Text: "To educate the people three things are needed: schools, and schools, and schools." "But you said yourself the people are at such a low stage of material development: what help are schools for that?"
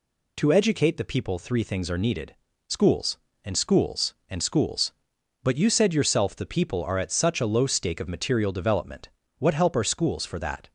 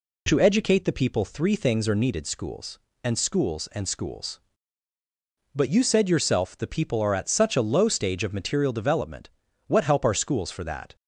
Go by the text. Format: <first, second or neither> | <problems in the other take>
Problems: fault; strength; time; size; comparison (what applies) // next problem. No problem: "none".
second | says "stake" for "stage"; at 7.6 s